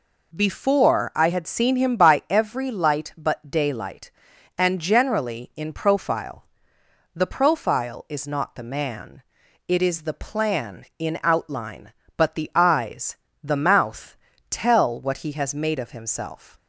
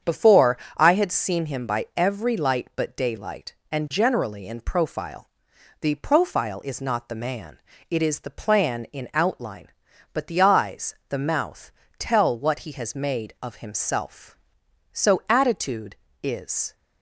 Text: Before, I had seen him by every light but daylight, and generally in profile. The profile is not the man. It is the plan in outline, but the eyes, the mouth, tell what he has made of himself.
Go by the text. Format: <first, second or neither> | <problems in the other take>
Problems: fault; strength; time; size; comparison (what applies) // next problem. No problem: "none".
first | starts louder than the rest; strong; until 1.2 s; 7.5 dB // goes on to say "So attitude is"; strong; from 14.9 s on; 1.8 s long